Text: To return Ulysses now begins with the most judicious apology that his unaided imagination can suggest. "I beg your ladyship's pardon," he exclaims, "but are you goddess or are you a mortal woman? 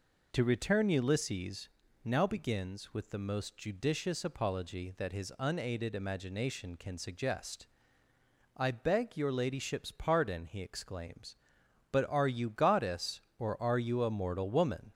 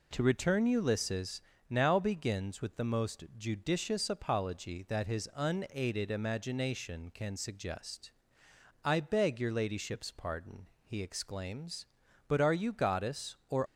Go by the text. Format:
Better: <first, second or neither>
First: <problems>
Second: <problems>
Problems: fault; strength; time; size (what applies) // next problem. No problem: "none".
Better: first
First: pauses between "Ulysses" and "now"; slight; at 1.6 s; 0.36 s long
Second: pauses between "Ulysses" and "now"; slight; at 1.3 s; 0.30 s long // stops before "are you a mortal woman"; at 13.6 s